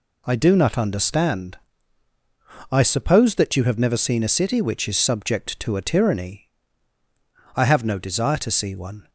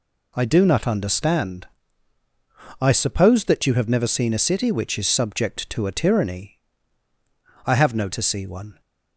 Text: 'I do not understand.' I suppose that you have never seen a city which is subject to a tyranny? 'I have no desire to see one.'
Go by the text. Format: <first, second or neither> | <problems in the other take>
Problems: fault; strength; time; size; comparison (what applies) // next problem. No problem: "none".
first | skips "desire"; at 8.0 s